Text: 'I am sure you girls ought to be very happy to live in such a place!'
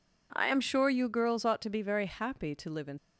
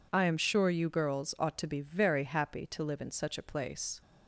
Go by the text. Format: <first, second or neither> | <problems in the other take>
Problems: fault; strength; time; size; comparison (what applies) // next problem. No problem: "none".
second | stops before "such a place"; at 2.9 s